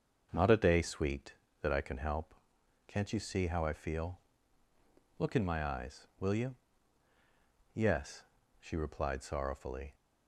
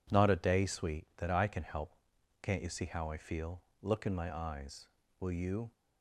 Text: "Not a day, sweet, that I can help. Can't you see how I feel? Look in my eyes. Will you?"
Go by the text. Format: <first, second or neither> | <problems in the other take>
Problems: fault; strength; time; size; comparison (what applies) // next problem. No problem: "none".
second | starts louder than the rest; until 1.3 s; 6.5 dB // goes on to say "Yes she replied sorrowfully"; strong; from 7.7 s on; 2.2 s long